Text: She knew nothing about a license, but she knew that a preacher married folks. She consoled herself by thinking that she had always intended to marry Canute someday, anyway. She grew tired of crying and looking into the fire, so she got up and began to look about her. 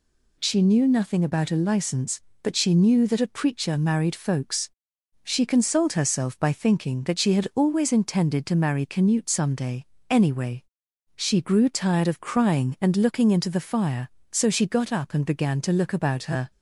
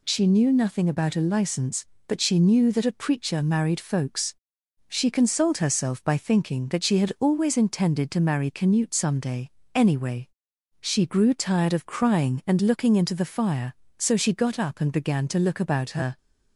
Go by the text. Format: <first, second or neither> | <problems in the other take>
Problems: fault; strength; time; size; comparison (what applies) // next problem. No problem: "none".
neither | none